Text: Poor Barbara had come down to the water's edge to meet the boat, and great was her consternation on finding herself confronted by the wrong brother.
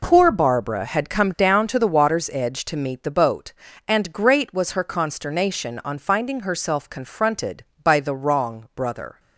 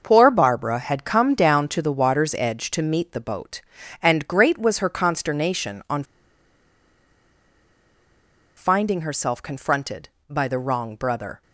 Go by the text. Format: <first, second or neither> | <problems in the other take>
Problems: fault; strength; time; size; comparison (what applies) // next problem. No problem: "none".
first | starts louder than the rest; until 1.0 s; 6 dB // pauses between "on" and "finding"; strong; at 6.0 s; 2.5 s long